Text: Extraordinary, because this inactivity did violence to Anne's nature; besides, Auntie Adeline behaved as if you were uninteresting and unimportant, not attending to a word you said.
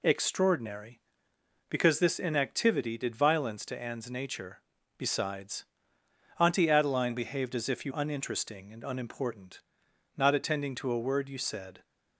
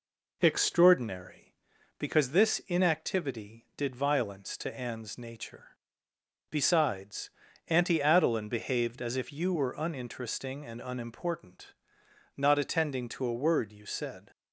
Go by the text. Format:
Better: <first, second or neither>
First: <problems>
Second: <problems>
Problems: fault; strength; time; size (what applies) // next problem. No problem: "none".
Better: second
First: skips "were"; at 7.9 s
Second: none